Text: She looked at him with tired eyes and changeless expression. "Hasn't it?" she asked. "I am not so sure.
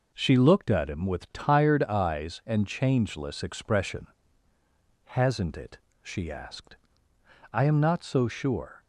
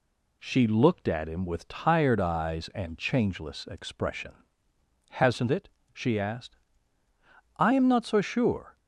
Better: neither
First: none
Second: none

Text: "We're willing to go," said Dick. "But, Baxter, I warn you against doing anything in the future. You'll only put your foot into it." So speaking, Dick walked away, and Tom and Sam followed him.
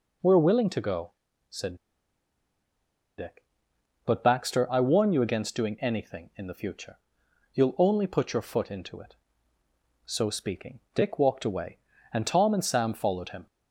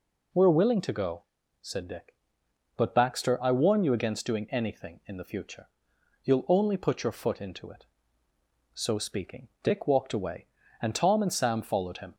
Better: second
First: pauses between "said" and "Dick"; strong; at 1.7 s; 1.4 s long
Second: none

